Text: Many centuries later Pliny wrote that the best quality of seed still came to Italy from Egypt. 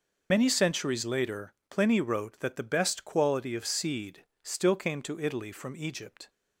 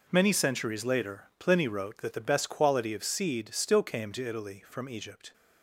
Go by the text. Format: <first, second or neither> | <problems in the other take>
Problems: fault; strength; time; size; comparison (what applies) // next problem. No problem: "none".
second | loses the start of "Many"; at 0.3 s; 80 ms // pauses between "later" and "Pliny"; slight; at 1.5 s; 0.16 s long // pauses between "seed" and "still"; slight; at 4.2 s; 0.18 s long